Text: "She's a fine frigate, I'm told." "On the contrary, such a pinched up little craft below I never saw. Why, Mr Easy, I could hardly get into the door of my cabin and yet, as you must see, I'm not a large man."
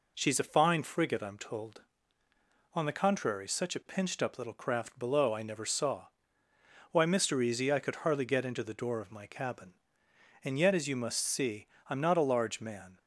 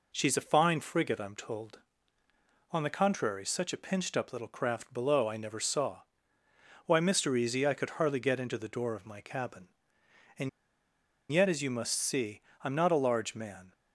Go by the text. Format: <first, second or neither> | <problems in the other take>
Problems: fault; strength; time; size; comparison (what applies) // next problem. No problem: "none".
first | pauses between "and" and "yet"; noticeable; at 10.4 s; 0.82 s long